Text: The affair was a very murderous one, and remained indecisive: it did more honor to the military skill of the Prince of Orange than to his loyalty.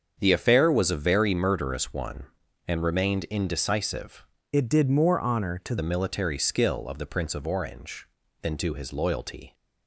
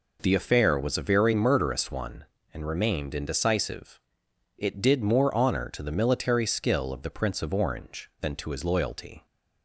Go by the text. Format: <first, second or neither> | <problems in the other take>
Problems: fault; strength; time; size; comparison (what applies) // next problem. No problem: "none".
second | starts louder than the rest; strong; until 1.2 s; 7 dB // changes voice from "it" to "to"; from 4.5 to 5.7 s; 1.2 s long